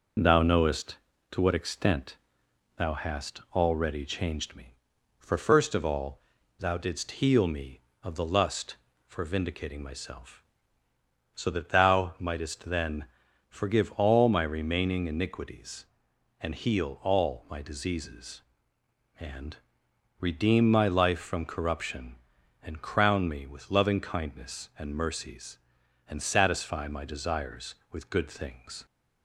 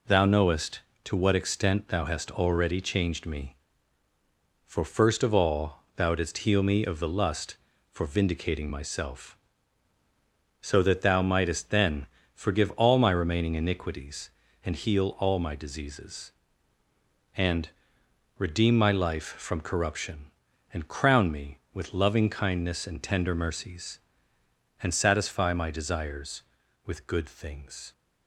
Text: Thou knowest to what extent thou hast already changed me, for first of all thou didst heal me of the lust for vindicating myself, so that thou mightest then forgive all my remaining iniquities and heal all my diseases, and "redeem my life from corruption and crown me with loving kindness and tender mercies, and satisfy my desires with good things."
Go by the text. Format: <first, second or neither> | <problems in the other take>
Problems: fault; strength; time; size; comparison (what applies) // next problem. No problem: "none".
second | pauses between "extent" and "thou"; noticeable; at 2.1 s; 0.60 s long // pauses between "all" and "thou"; at 6.2 s; 0.38 s long // pauses between "then" and "forgive"; at 13.0 s; 0.44 s long; slight in the second // pauses between "and" and "redeem"; noticeable; at 19.5 s; 0.62 s long; noticeable in the second // skips "tender"; at 24.9 s